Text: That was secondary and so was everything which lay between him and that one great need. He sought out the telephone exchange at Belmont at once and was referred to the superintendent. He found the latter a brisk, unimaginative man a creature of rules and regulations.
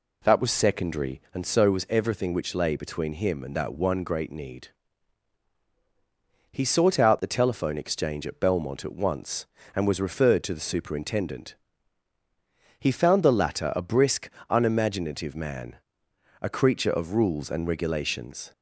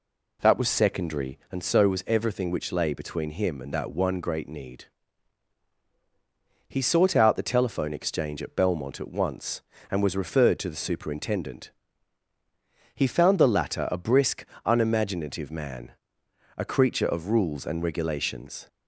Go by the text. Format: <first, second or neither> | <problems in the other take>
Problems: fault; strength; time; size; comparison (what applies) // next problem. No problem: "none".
neither | pauses between "man" and "a"; noticeable; the same in both